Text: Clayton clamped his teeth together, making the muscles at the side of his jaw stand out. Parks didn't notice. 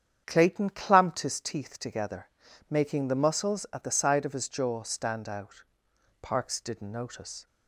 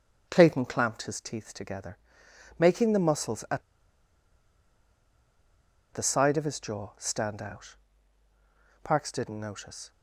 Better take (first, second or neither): first